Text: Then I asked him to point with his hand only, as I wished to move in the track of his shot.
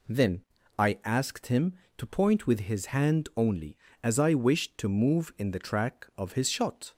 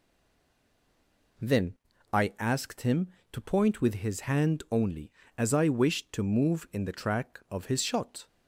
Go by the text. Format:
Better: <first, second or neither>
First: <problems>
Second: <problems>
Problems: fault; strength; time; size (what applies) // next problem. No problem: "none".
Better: first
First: pauses between "Then" and "I"; slight; at 0.4 s; 0.36 s long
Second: stays silent before the first word; noticeable; until 1.3 s; 1.3 s long // pauses between "Then" and "I"; at 1.7 s; 0.38 s long